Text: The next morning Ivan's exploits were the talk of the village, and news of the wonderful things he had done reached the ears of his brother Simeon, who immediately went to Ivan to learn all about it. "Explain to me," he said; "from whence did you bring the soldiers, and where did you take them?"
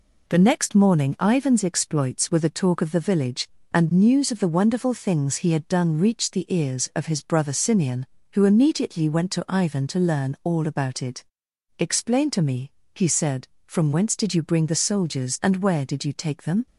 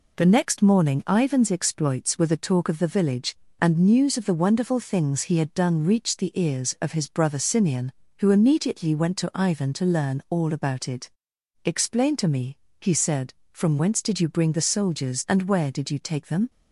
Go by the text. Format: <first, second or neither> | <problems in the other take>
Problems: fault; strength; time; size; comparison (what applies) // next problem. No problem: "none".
neither | none